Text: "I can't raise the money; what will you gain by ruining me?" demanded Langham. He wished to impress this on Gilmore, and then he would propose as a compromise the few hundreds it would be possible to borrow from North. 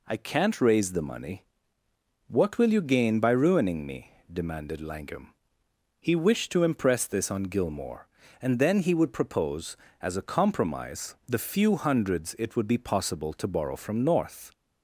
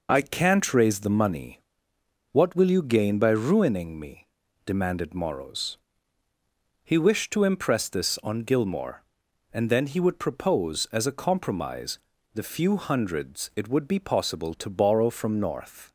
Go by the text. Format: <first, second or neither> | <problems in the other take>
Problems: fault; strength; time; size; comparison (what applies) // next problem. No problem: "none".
first | says "Morrows" for "Langham"; at 5.1 s // pauses between "compromise" and "the"; slight; at 12.0 s; 0.34 s long